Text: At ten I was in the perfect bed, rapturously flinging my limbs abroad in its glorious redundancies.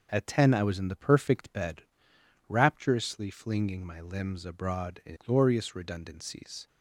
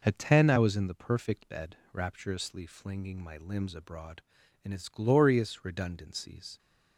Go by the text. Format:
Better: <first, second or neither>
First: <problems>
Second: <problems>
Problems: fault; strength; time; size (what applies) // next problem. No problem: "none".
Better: second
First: skips "its"; at 5.1 s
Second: none